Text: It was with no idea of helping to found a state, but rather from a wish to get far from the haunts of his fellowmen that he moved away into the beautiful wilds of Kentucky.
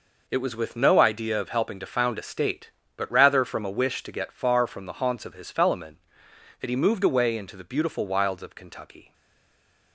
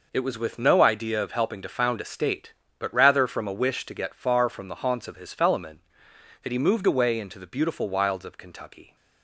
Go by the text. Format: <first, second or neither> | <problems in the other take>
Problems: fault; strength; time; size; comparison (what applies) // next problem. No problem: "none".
second | stays silent after the last word; slight; from 9.1 s on; 0.8 s long